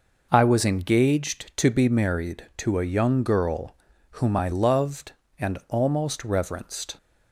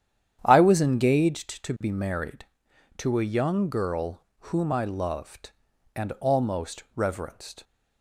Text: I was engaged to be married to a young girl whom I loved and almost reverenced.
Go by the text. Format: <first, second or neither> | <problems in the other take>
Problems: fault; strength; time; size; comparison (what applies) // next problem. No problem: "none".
first | starts louder than the rest; strong; until 1.4 s; 9.5 dB // pauses between "girl" and "whom"; slight; at 4.2 s; 0.26 s long; slight in the first